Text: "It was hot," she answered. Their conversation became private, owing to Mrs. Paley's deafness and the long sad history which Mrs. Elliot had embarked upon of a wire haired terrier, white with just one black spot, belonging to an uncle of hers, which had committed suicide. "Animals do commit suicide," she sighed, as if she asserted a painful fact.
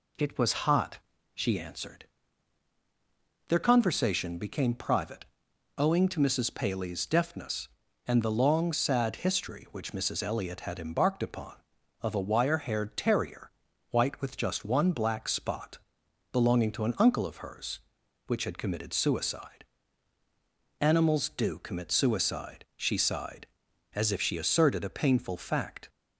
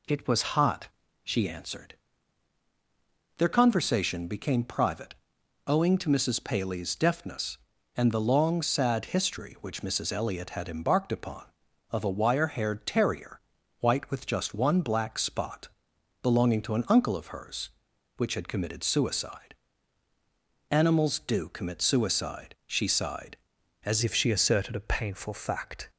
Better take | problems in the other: first | changes voice at "if"; from 24.0 s on; 1.8 s long

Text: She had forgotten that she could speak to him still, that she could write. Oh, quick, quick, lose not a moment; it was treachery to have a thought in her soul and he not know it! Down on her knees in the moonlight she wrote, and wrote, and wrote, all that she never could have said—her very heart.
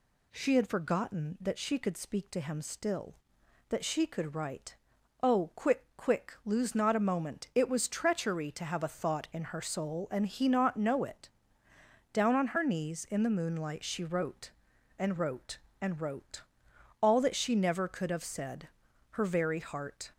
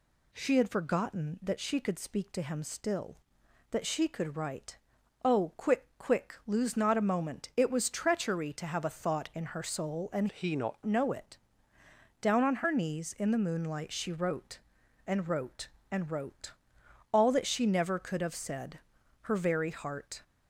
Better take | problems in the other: first | changes voice from "he" to "not"; from 10.3 to 10.8 s; 0.5 s long

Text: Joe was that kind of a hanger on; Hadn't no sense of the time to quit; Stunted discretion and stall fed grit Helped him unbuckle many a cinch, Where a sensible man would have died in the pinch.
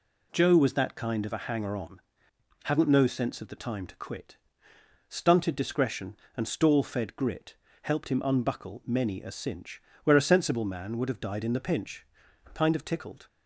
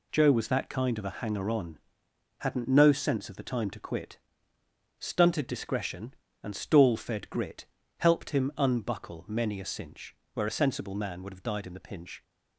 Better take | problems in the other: second | pauses between "grit" and "Helped"; slight; at 7.5 s; 0.26 s long; slight in the second // goes on to say "Kind of tickled"; noticeable; from 12.5 s on; 0.74 s long

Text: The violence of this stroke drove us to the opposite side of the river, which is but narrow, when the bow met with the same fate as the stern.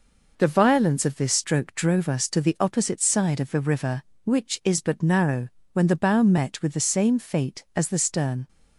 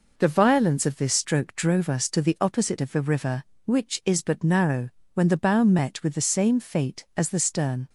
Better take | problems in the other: first | skips "side"; at 2.7 s

